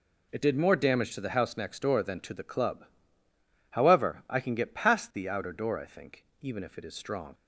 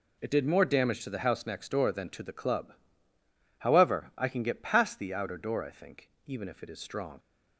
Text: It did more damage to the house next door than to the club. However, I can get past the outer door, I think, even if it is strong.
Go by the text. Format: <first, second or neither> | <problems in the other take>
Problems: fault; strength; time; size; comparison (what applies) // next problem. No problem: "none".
neither | none